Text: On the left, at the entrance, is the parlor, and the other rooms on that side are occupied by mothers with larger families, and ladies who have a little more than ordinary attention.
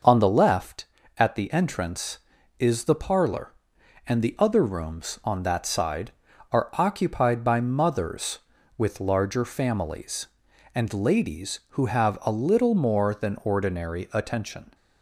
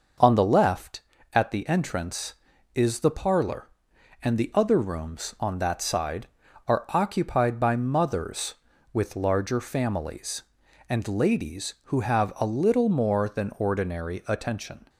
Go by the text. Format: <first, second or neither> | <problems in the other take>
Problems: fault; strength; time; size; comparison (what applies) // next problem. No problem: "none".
neither | starts louder than the rest; noticeable; the same in both